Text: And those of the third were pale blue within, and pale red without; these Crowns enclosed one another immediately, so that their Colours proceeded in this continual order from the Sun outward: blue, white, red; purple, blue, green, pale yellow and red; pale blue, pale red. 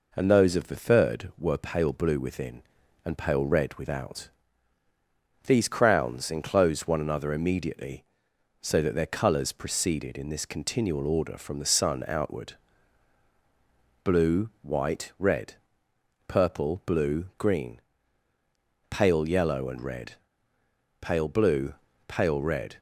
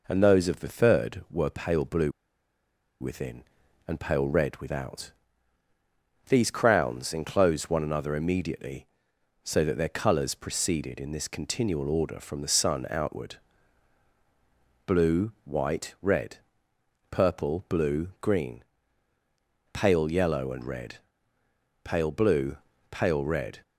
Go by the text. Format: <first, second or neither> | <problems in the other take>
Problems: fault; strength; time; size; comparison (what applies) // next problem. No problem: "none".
first | pauses between "blue" and "within"; noticeable; at 2.1 s; 0.89 s long